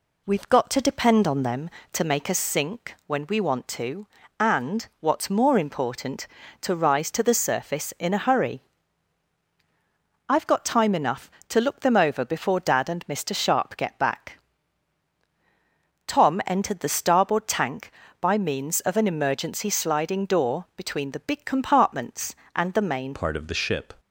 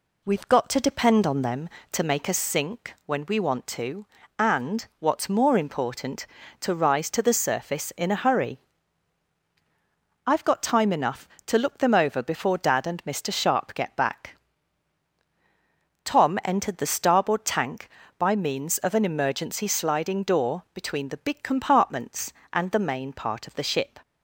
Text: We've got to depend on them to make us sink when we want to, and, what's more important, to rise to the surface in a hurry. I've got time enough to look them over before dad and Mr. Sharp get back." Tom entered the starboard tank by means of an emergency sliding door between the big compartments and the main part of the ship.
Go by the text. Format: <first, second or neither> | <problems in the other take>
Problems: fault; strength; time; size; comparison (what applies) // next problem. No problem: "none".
second | changes voice at "part"; from 23.1 s on; 0.8 s long